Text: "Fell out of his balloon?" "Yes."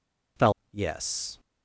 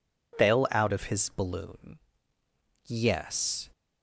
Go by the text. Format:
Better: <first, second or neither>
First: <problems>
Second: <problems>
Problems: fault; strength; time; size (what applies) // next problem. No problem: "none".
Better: second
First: skips "out of his balloon"; at 0.6 s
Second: none